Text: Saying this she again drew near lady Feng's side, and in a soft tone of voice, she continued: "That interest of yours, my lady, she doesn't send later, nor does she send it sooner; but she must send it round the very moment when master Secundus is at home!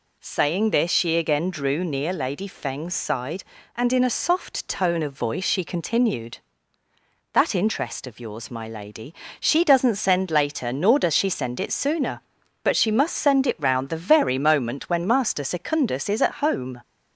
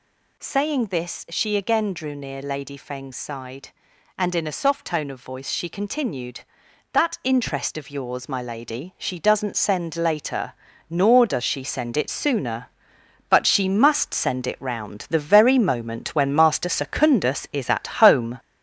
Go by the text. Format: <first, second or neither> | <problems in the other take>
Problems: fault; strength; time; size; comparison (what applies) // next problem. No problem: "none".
first | gets louder; noticeable; throughout; 5.5 dB // pauses between "at" and "home"; slight; at 17.8 s; 0.16 s long